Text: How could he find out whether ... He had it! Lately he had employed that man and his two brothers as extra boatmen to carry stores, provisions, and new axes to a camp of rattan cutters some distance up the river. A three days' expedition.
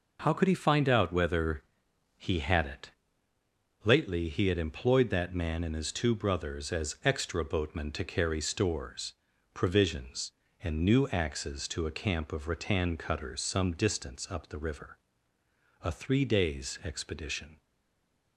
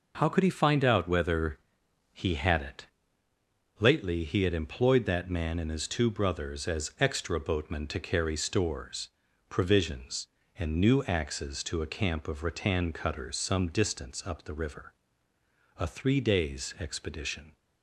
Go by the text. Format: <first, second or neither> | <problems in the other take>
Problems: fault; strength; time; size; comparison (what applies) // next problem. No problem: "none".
second | stays silent after the last word; slight; from 17.6 s on; 0.7 s long